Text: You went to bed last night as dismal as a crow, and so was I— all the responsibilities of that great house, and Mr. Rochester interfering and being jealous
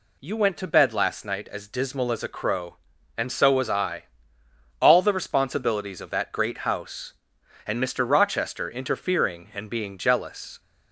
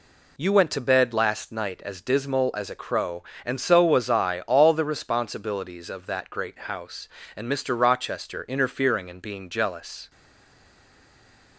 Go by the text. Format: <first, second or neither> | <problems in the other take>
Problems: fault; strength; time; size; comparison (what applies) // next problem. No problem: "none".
first | stays silent after the last word; noticeable; from 10.1 s on; 1.4 s long